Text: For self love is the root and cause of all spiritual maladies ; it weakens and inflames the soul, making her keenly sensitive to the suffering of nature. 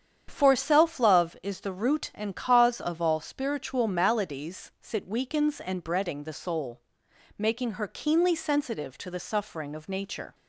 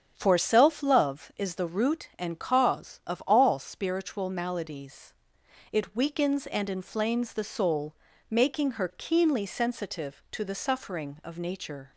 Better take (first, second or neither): second